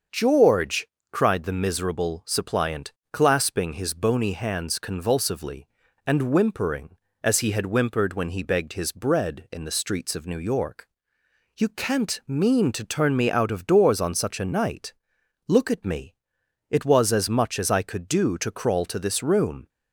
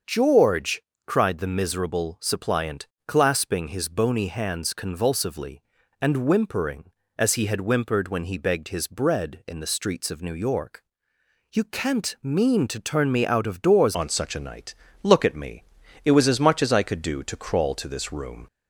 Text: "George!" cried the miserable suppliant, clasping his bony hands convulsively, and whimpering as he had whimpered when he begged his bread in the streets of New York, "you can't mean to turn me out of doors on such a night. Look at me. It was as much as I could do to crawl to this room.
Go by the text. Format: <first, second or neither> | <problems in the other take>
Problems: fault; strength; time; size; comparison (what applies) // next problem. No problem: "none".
first | starts louder than the rest; until 1.3 s; 6.5 dB; also in the first // changes voice at "on"; from 13.9 s on; 4.5 s long